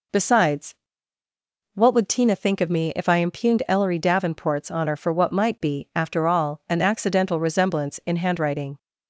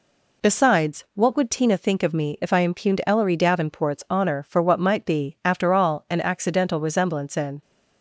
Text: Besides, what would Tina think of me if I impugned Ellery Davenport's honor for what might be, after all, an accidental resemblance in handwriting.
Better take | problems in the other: first | stops before "handwriting"; at 7.6 s

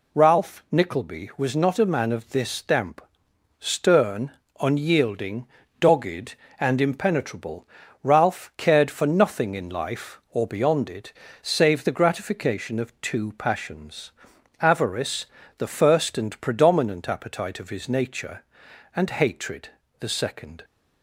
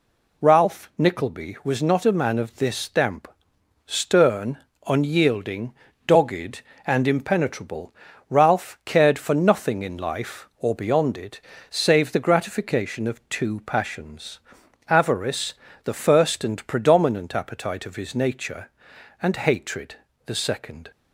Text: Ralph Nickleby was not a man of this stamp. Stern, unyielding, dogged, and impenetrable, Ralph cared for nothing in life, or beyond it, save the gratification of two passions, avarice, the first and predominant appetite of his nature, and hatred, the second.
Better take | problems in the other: neither | none

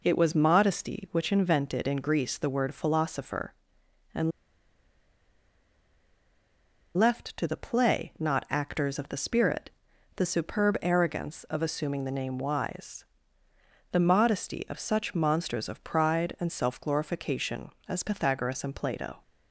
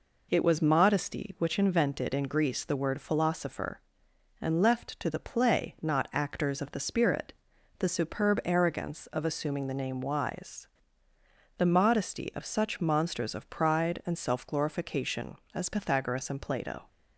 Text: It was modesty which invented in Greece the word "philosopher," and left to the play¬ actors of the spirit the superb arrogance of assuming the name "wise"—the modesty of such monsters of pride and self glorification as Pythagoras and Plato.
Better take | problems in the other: second | pauses between "and" and "left"; strong; at 4.3 s; 2.6 s long // pauses between "spirit" and "the"; noticeable; at 9.6 s; 0.46 s long; noticeable in the second

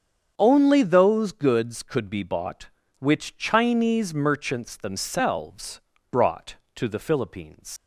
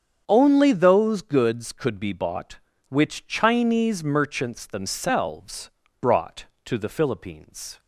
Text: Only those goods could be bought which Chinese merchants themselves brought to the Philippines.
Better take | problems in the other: second | starts louder than the rest; strong; until 1.3 s; 7.5 dB; strong in the second // pauses between "themselves" and "brought"; slight; at 5.7 s; 0.32 s long; slight in the second // leaves "Philippines" unfinished; at 7.7 s; 130 ms

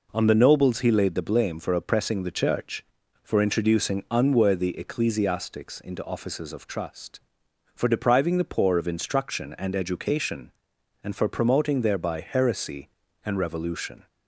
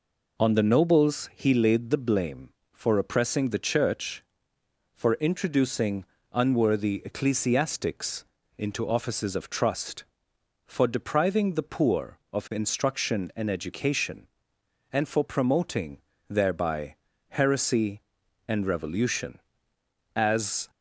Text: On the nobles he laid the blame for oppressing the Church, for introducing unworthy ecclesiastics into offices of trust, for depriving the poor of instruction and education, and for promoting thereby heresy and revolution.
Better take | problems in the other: first | pauses between "introducing" and "unworthy"; slight; at 6.0 s; 0.26 s long // pauses between "ecclesiastics" and "into"; slight; at 8.2 s; 0.34 s long // pauses between "promoting" and "thereby"; slight; at 15.9 s; 0.30 s long // pauses between "thereby" and "heresy"; slight; at 16.9 s; 0.32 s long // goes on to say "As"; from 20.1 s on; 0.54 s long

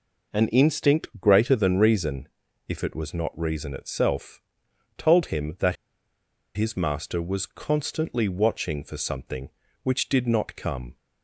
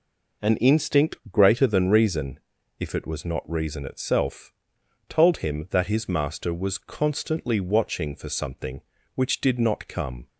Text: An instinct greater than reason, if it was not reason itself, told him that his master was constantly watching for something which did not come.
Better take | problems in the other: second | pauses between "that" and "his"; noticeable; at 5.7 s; 0.80 s long

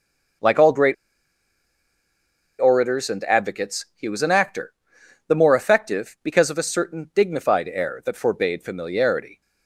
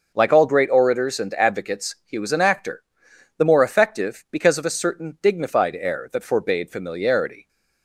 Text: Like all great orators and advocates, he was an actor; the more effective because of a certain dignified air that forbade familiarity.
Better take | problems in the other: second | pauses between "great" and "orators"; strong; at 0.9 s; 1.6 s long

